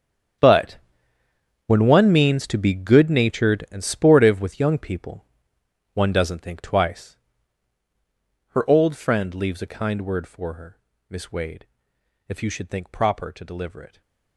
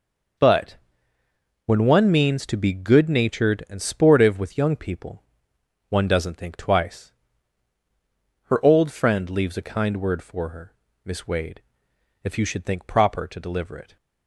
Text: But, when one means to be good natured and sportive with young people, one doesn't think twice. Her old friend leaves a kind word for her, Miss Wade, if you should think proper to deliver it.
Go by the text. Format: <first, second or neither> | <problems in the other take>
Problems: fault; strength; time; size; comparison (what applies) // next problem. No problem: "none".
second | gets quieter; strong; throughout; 17 dB